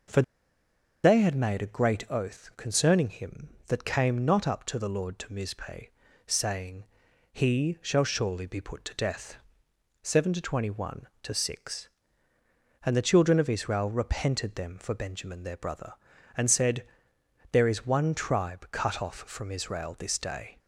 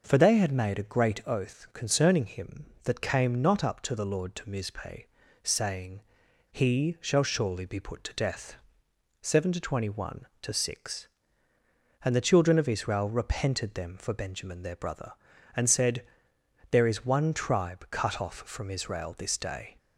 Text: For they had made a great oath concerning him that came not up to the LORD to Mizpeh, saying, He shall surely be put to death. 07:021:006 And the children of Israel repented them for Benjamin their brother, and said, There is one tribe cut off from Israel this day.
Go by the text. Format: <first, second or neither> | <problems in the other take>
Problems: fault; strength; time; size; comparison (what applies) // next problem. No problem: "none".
second | pauses between "For" and "they"; noticeable; at 0.2 s; 0.81 s long